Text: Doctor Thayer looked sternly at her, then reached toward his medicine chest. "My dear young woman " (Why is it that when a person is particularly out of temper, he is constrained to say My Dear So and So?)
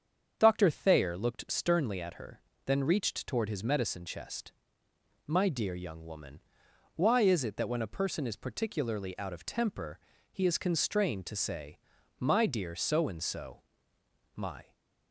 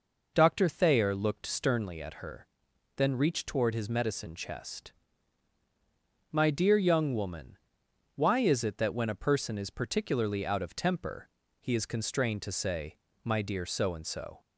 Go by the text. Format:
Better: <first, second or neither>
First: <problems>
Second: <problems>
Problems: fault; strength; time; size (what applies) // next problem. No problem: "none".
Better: second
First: starts louder than the rest; strong; until 1.3 s; 7.5 dB // pauses between "say" and "My"; at 11.7 s; 0.40 s long // goes on to say "My"; slight; from 14.3 s on; 0.40 s long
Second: pauses between "say" and "My"; slight; at 12.9 s; 0.26 s long